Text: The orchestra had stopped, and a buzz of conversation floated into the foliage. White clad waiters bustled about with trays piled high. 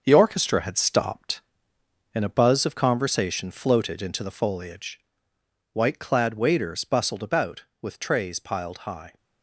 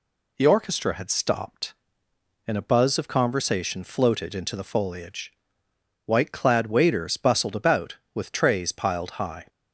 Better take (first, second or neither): second